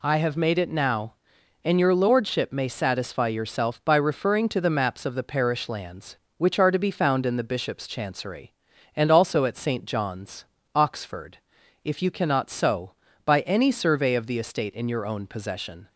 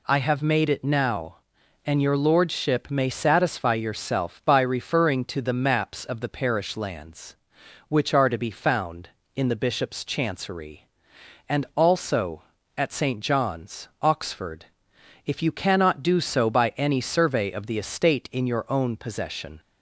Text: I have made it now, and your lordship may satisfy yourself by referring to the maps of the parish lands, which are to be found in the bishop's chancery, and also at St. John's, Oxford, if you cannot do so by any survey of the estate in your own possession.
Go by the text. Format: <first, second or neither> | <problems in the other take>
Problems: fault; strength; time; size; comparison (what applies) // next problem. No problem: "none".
second | skips "do"; at 12.4 s